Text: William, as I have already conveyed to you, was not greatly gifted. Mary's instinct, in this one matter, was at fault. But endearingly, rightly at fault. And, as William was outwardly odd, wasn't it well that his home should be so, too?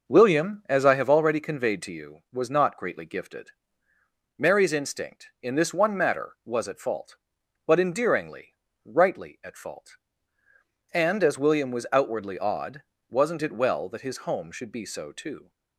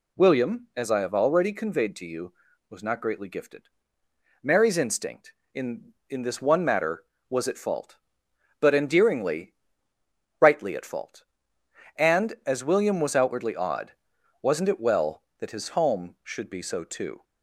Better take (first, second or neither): first